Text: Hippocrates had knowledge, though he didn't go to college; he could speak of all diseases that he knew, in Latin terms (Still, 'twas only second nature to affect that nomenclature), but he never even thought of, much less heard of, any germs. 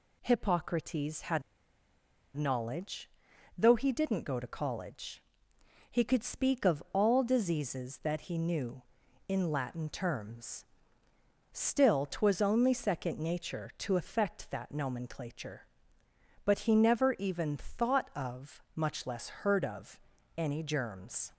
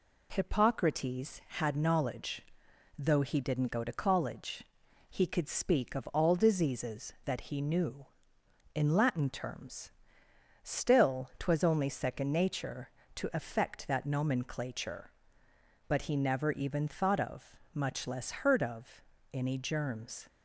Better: second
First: pauses between "had" and "knowledge"; noticeable; at 1.4 s; 0.94 s long // pauses between "less" and "heard"; slight; at 19.2 s; 0.16 s long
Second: none

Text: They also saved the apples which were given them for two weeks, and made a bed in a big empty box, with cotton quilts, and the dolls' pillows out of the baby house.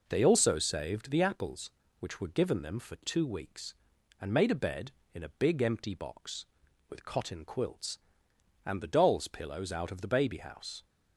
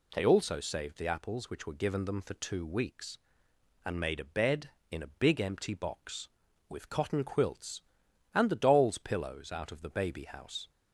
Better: neither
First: none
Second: none

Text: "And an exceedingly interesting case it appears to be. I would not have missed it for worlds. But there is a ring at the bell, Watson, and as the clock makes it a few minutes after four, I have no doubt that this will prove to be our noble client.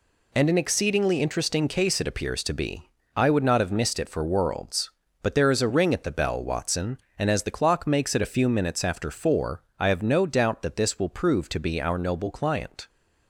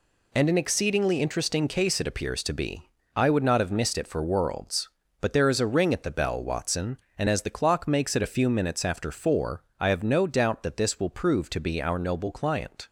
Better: neither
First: none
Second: none

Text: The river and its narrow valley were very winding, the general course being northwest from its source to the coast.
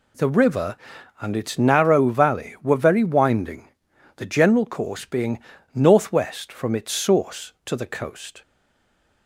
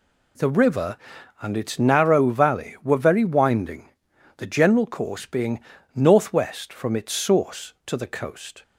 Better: second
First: pauses between "being" and "northwest"; slight; at 5.3 s; 0.34 s long // stays silent after the last word; slight; from 8.4 s on; 0.8 s long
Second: pauses between "being" and "northwest"; slight; at 5.6 s; 0.34 s long

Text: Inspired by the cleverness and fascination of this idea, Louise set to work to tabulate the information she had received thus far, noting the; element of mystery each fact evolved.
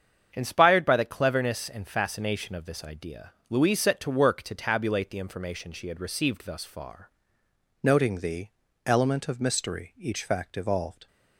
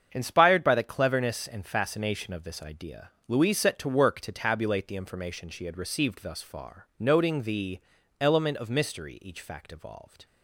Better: second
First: starts louder than the rest; strong; until 1.3 s; 7.5 dB // changes voice at "noting"; from 7.8 s on; 3.2 s long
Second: starts louder than the rest; strong; until 1.1 s; 7.5 dB

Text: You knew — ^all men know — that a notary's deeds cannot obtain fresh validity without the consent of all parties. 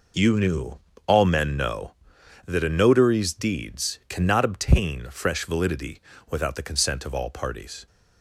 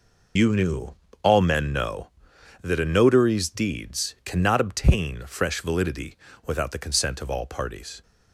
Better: first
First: pauses between "validity" and "without"; slight; at 5.9 s; 0.32 s long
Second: loses the start of "You"; at 0.3 s; 35 ms // pauses between "validity" and "without"; slight; at 6.1 s; 0.32 s long

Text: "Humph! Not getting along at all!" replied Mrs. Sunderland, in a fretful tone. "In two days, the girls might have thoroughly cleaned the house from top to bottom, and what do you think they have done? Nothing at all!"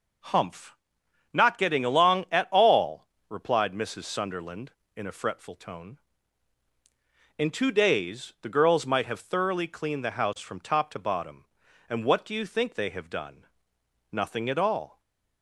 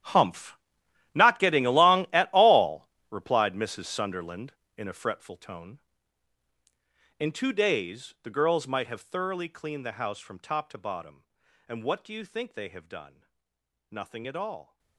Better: first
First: none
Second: gets quieter; strong; throughout; 17.5 dB

